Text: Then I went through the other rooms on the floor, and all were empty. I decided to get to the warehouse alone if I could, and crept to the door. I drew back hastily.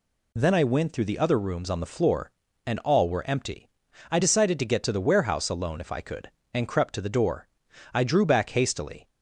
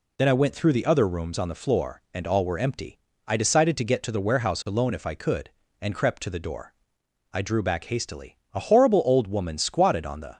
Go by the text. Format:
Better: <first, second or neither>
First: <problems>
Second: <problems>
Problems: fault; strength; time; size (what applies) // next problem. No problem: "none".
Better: first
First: none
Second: goes on to say "A horrible old woman squatted on the"; strong; from 8.5 s on; 1.8 s long